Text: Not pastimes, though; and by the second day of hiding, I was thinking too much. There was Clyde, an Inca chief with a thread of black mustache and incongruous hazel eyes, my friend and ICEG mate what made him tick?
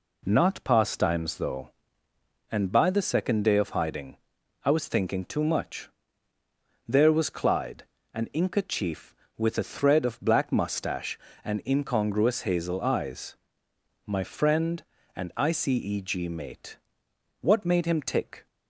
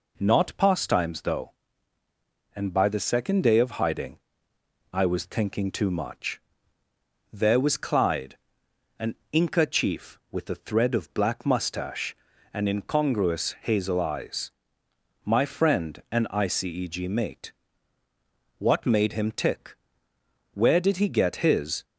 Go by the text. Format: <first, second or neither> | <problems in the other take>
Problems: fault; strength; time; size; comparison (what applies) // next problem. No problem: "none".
first | pauses between "an" and "Inca"; slight; at 9.1 s; 0.16 s long // pauses between "mate" and "what"; at 17.5 s; 1.0 s long; noticeable in the first // goes on to say "Where did he get his"; noticeable; from 20.5 s on; 1.3 s long